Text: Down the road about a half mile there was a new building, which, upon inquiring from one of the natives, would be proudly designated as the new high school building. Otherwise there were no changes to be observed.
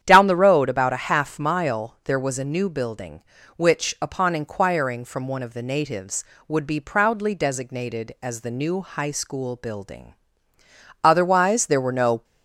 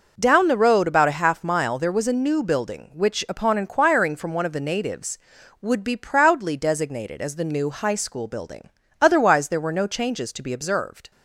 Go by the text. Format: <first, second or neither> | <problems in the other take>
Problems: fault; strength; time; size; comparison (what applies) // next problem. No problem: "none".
second | starts louder than the rest; strong; until 1.0 s; 9.5 dB // stops before "changes to be observed"; at 12.2 s